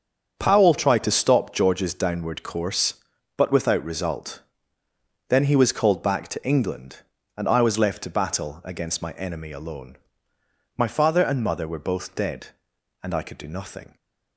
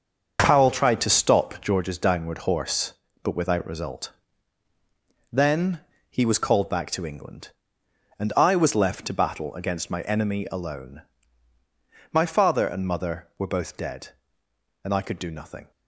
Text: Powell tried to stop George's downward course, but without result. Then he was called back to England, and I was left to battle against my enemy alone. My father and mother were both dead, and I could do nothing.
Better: first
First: starts louder than the rest; strong; until 1.3 s; 7 dB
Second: starts louder than the rest; until 1.4 s; 7 dB // says "horse" for "course"; at 2.3 s // pauses between "Then" and "he"; slight; at 5.8 s; 0.28 s long

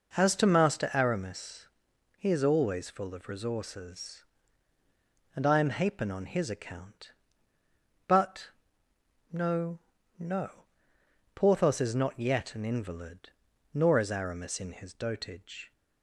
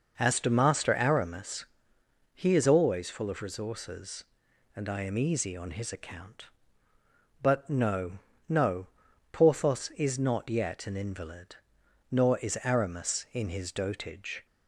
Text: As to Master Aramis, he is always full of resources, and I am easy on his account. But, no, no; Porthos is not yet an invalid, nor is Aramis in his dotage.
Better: second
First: says "hapen" for "easy"; at 5.6 s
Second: none

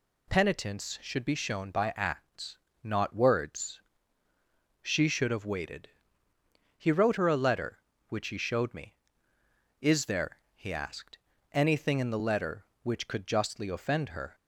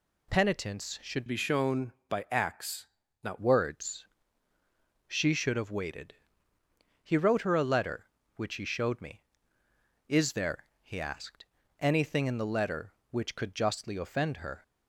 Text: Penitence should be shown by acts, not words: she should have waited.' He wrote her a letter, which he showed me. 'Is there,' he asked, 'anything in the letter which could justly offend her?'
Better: first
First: none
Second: changes voice from "be" to "not"; from 1.2 to 3.3 s; 2.1 s long

